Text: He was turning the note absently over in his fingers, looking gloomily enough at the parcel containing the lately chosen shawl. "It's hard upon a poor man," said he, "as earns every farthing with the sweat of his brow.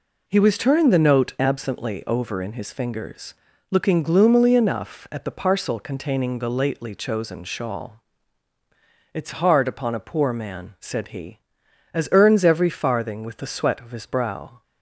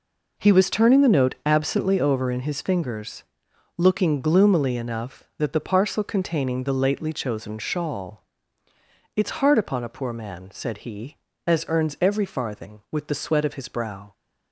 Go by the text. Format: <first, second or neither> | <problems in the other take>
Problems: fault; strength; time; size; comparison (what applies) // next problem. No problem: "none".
first | says "that" for "at"; at 5.3 s